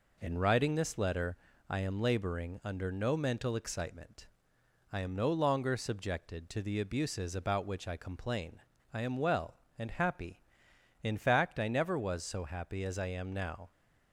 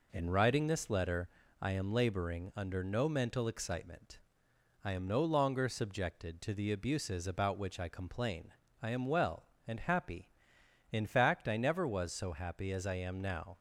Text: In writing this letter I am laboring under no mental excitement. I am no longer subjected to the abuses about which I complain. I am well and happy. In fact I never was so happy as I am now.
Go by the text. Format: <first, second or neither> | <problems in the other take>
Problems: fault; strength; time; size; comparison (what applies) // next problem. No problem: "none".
neither | pauses between "letter" and "I"; slight; the same in both